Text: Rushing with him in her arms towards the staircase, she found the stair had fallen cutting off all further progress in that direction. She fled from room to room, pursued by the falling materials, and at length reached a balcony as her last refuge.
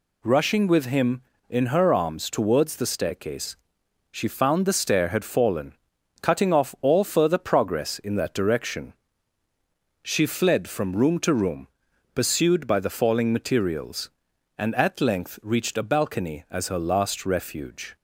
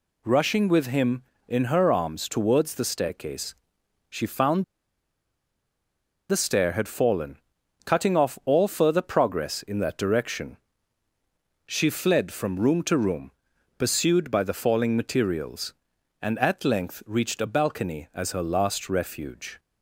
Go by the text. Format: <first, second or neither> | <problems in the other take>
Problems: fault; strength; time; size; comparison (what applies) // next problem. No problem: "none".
first | pauses between "found" and "the"; strong; at 4.6 s; 1.6 s long // pauses between "fallen" and "cutting"; noticeable; at 7.3 s; 0.46 s long; noticeable in the first